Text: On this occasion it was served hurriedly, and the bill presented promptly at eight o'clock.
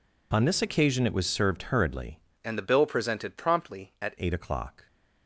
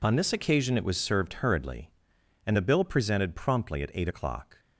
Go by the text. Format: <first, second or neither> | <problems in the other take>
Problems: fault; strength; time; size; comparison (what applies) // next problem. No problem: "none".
second | changes voice from "and" to "at"; from 2.4 to 4.1 s; 1.7 s long